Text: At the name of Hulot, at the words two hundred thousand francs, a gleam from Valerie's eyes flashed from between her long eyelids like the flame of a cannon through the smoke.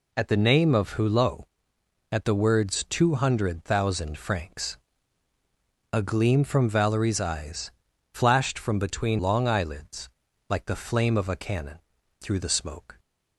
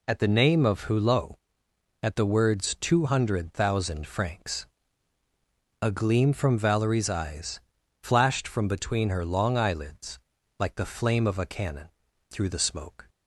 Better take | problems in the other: second | pauses between "eyes" and "flashed"; at 7.7 s; 0.38 s long; also in the second // skips "her"; at 9.1 s // pauses between "eyelids" and "like"; at 10.0 s; 0.40 s long; also in the second // pauses between "cannon" and "through"; at 11.7 s; 0.42 s long; also in the second

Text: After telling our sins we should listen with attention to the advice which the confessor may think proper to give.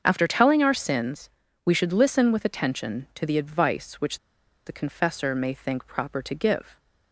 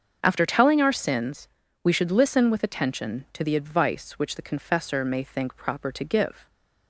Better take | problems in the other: second | starts louder than the rest; until 1.0 s; 7 dB; also in the second // pauses between "sins" and "we"; slight; at 1.2 s; 0.34 s long; slight in the second // pauses between "which" and "the"; noticeable; at 4.1 s; 0.47 s long

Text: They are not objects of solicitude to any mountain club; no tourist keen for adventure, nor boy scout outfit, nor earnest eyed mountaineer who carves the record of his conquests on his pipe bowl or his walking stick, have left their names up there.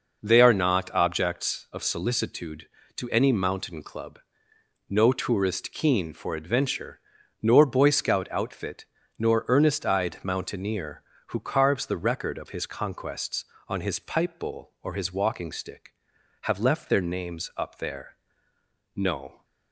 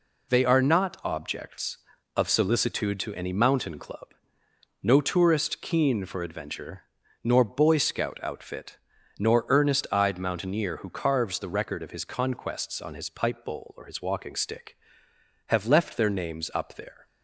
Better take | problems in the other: second | goes on to say "No"; slight; from 18.9 s on; 0.48 s long

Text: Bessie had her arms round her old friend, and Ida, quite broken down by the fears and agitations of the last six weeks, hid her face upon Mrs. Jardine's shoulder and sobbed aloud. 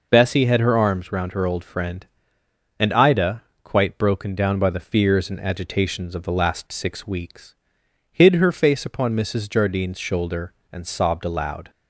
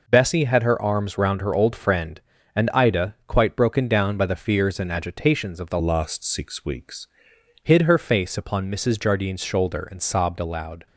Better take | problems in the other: first | changes voice from "last" to "weeks"; from 5.8 to 7.0 s; 1.2 s long

